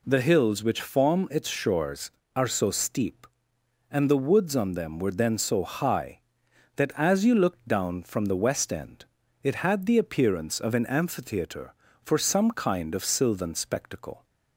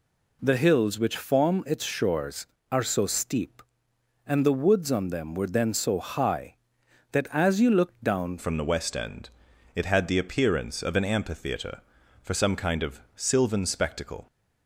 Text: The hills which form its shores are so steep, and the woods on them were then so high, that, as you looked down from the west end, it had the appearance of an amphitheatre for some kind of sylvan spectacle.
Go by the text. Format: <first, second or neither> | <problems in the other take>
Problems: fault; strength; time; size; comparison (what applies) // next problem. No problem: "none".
first | changes voice at "from"; from 8.3 s on; 5.9 s long // pauses between "of" and "sylvan"; slight; at 12.9 s; 0.18 s long